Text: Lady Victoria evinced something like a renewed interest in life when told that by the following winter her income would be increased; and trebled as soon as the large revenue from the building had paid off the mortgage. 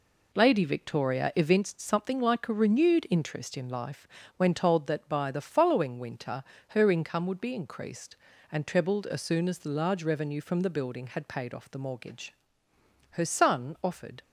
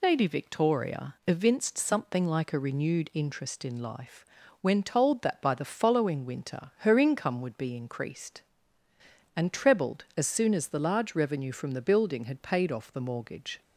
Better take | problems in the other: second | pauses between "life" and "when"; slight; at 4.0 s; 0.30 s long; slight in the second // pauses between "winter" and "her"; slight; at 6.4 s; 0.26 s long // goes on to say "Her son offered"; noticeable; from 13.0 s on; 1.1 s long

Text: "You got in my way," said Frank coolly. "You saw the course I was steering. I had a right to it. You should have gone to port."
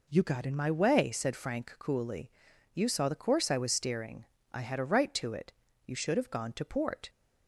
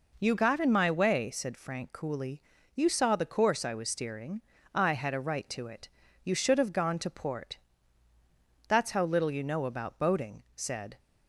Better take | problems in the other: first | goes on to say "That's how little you know about boating said"; strong; from 8.6 s on; 2.3 s long

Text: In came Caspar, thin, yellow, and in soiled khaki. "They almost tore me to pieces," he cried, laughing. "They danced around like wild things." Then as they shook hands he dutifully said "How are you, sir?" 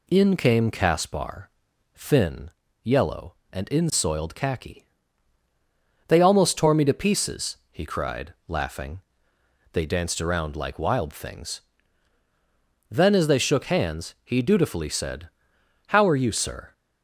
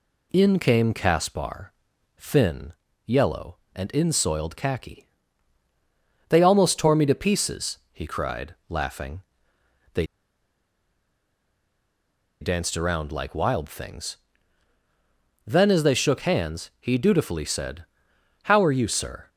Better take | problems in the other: first | pauses between "They" and "danced"; strong; at 10.0 s; 2.3 s long // pauses between "said" and "How"; noticeable; at 17.8 s; 0.60 s long; noticeable in the first

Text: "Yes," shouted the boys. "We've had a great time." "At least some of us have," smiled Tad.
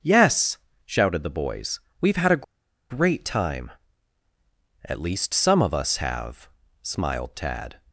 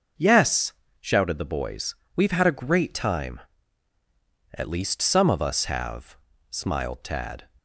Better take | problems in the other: second | starts louder than the rest; noticeable; until 1.3 s; 6 dB // pauses between "a" and "great"; noticeable; at 2.4 s; 0.46 s long

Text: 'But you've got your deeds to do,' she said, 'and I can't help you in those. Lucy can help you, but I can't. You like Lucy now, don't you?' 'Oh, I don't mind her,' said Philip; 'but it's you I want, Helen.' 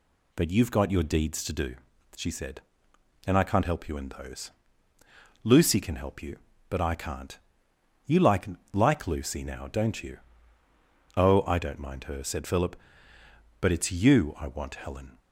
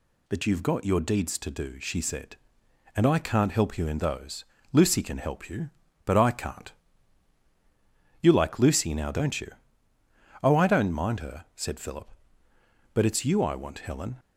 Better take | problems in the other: second | says "like" twice; at 8.7 s

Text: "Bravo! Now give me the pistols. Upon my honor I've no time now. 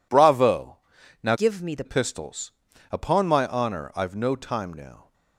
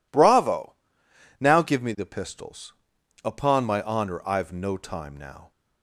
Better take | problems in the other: second | changes voice from "give" to "the"; from 1.3 to 1.8 s; 0.5 s long

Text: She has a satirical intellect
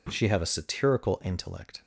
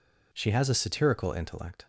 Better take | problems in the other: second | says "have" for "has"; at 0.2 s

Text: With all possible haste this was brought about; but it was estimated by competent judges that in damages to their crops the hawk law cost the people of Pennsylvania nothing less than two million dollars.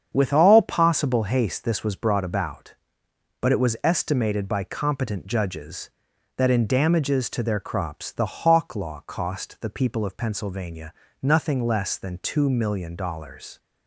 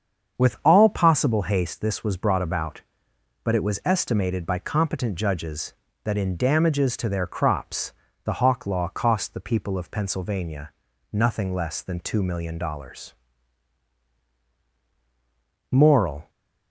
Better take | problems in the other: first | starts louder than the rest; strong; until 1.4 s; 7 dB; strong in the first // pauses between "crops" and "the"; slight; at 7.9 s; 0.32 s long // pauses between "Pennsylvania" and "nothing"; at 10.7 s; 0.38 s long; slight in the first // goes on to say "Moral"; from 15.7 s on; 0.58 s long

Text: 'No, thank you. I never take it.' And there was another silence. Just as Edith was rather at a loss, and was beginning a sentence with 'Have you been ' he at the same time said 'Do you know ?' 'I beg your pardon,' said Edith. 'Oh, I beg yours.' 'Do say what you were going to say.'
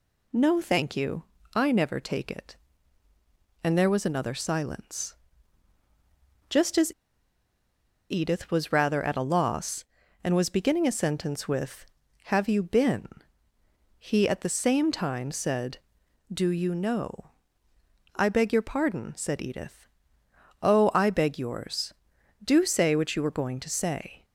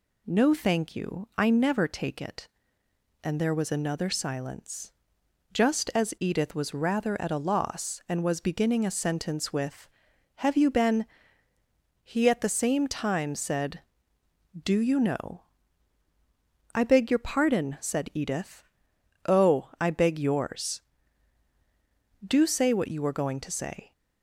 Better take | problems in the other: second | pauses between "as" and "Edith"; at 6.9 s; 1.1 s long

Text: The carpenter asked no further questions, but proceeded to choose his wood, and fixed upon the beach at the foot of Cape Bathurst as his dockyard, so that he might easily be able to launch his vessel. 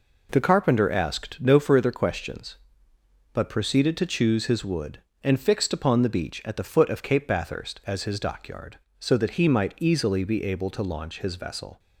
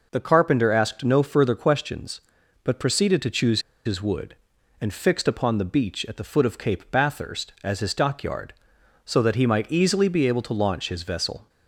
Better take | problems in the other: first | pauses between "choose" and "his"; slight; at 3.6 s; 0.24 s long

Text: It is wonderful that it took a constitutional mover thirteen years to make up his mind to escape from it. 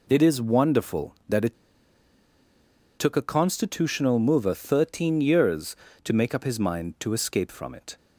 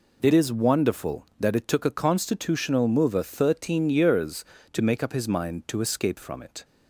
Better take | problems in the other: second | pauses between "it" and "took"; strong; at 1.5 s; 1.4 s long

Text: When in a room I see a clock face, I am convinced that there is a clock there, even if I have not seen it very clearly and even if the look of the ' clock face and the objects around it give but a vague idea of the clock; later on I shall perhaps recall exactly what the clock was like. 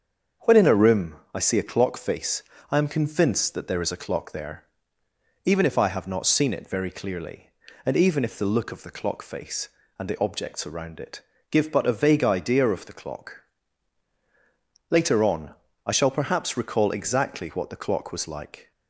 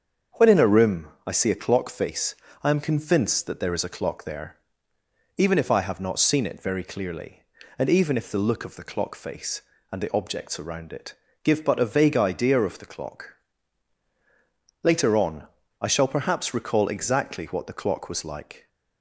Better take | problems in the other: neither | starts louder than the rest; the same in both // pauses between "room" and "I"; slight; the same in both // pauses between "it" and "give"; slight; the same in both // pauses between "on" and "I"; slight; the same in both

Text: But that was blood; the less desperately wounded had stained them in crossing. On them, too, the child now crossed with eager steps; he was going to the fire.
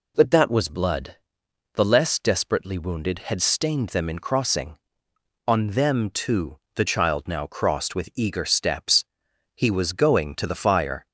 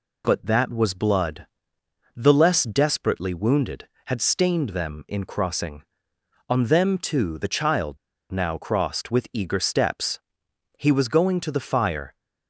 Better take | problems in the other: first | pauses between "child" and "now"; slight; at 7.9 s; 0.34 s long

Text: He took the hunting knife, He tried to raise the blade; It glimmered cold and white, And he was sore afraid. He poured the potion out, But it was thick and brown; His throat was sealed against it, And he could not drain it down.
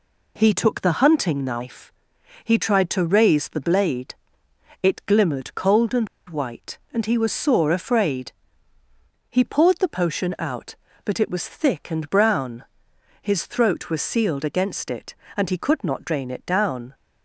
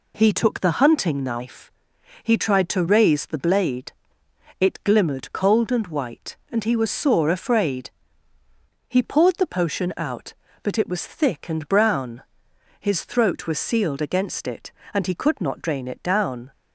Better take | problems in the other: second | pauses between "and" and "white"; slight; at 6.0 s; 0.22 s long

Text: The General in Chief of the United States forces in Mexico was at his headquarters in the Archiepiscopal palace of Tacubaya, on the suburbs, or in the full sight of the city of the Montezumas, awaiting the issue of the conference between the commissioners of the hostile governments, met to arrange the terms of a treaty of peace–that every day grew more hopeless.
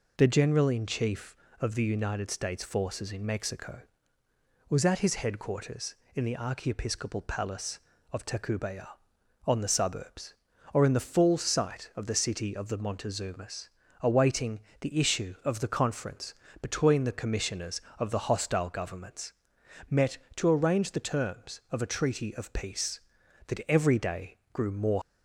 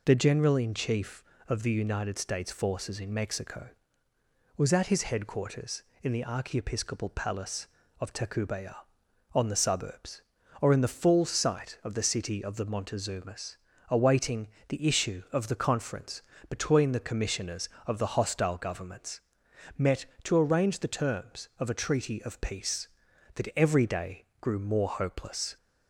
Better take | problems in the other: second | pauses between "awaiting" and "the"; slight; at 14.6 s; 0.20 s long; slight in the second // pauses between "conference" and "between"; slight; at 16.3 s; 0.26 s long; slight in the second // pauses between "day" and "grew"; slight; at 24.3 s; 0.16 s long; slight in the second // stops before "hopeless"; at 25.0 s

